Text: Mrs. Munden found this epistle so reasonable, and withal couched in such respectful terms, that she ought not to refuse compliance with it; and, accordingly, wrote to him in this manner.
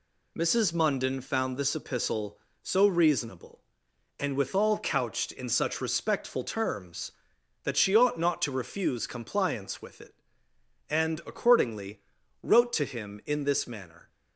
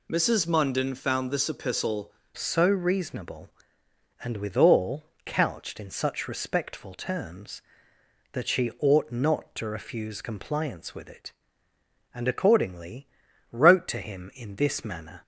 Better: first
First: none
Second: changes voice at "so"; from 2.3 s on; 12.9 s long // pauses between "withal" and "couched"; slight; at 5.0 s; 0.22 s long

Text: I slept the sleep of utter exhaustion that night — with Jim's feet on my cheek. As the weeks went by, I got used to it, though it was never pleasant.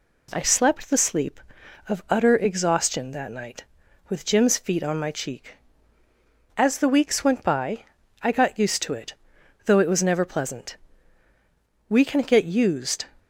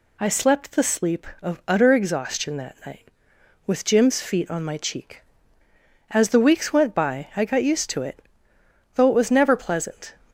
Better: second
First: goes on to say "We can get used"; noticeable; from 11.8 s on; 1.1 s long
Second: none

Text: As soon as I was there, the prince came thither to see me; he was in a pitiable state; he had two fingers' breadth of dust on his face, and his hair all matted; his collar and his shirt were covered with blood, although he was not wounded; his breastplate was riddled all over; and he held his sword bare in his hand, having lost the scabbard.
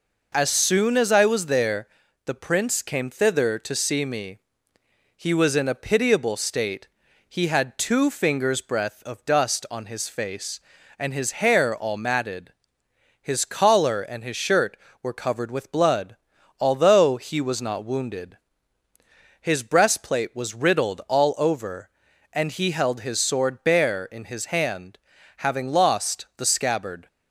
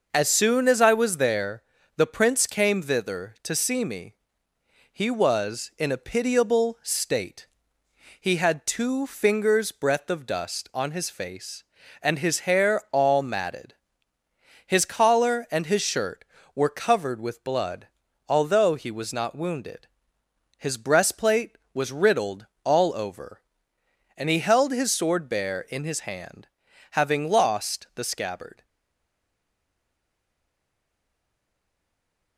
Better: first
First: none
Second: pauses between "riddled" and "all"; slight; at 22.4 s; 0.18 s long // stays silent after the last word; strong; from 28.6 s on; 3.7 s long

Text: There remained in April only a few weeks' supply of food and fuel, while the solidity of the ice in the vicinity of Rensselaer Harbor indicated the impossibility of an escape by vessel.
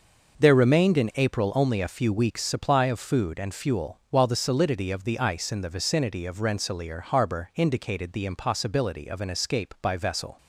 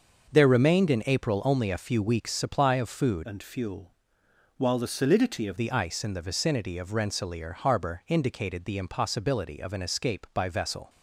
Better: first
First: none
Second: starts louder than the rest; until 1.3 s; 6.5 dB // changes voice from "and" to "of"; from 3.2 to 5.5 s; 2.3 s long

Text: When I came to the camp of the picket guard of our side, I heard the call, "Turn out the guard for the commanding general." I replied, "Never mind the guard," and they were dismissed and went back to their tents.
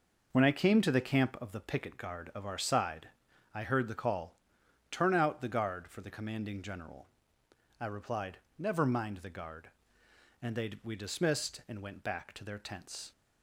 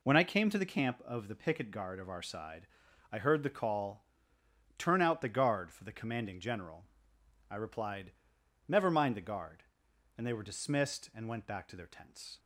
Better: second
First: says "we" for "were"; at 10.8 s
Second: none

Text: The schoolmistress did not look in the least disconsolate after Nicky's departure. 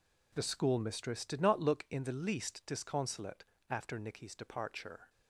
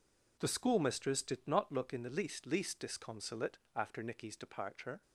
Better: first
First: pauses between "disconsolate" and "after"; slight; at 3.4 s; 0.26 s long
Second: says "least" twice; at 2.4 s // pauses between "disconsolate" and "after"; slight; at 3.5 s; 0.18 s long

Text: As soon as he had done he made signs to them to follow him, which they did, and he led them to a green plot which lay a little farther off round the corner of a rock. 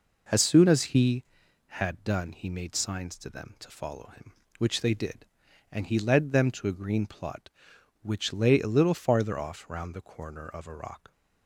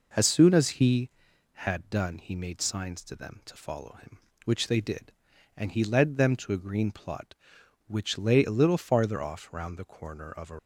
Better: first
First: none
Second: stops before "rock"; at 10.5 s

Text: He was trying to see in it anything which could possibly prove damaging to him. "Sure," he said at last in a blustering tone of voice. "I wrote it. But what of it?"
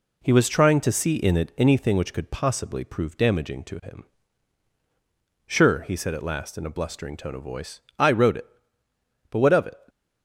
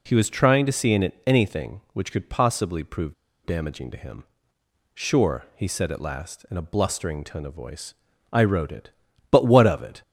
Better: first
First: none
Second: pauses between "prove" and "damaging"; slight; at 3.1 s; 0.31 s long

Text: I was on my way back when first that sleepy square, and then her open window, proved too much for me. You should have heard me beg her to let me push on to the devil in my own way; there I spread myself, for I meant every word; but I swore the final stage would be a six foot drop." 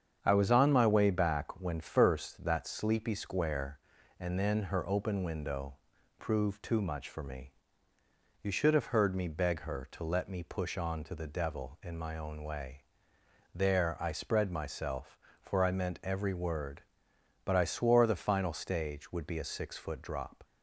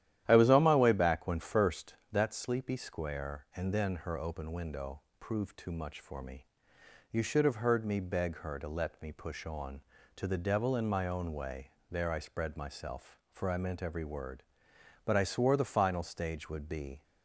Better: first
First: starts louder than the rest; strong; until 1.2 s; 7.5 dB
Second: starts louder than the rest; strong; until 1.2 s; 12 dB // stops before "a six foot drop"; at 17.0 s

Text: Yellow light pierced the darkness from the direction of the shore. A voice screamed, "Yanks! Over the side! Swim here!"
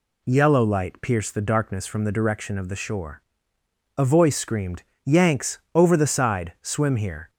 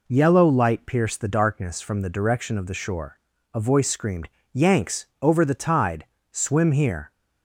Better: first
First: none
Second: says "tide" for "side"; at 5.5 s

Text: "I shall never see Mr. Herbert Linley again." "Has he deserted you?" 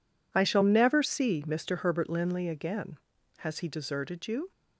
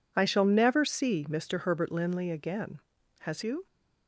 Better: first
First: none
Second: skips "he deserted"; at 3.4 s

